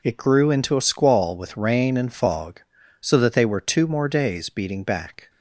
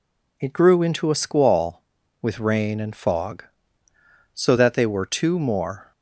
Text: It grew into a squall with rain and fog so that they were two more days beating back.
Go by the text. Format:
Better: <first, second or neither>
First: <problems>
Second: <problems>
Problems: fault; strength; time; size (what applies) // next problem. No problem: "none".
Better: first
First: none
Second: stops before "days beating back"; at 5.9 s